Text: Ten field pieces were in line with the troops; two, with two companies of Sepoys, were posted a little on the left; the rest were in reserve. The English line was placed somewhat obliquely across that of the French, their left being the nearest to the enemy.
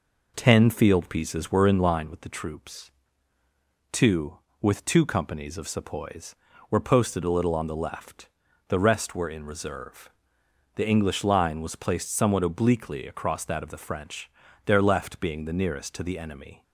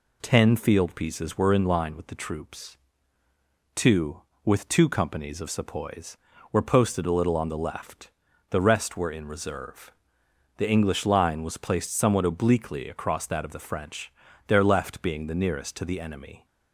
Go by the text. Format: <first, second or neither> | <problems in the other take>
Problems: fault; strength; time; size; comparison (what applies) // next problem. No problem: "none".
second | starts louder than the rest; noticeable; until 2.2 s; 4.5 dB